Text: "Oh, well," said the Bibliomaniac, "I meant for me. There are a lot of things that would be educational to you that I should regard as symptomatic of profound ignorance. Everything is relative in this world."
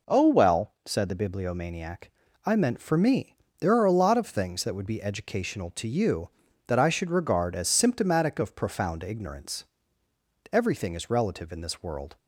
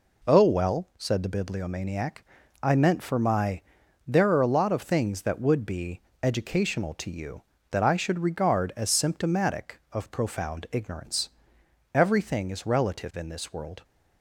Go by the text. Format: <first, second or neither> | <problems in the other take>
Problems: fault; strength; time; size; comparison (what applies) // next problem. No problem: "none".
first | says "my" for "me"; at 3.1 s // pauses between "be" and "educational"; slight; at 5.9 s; 0.24 s long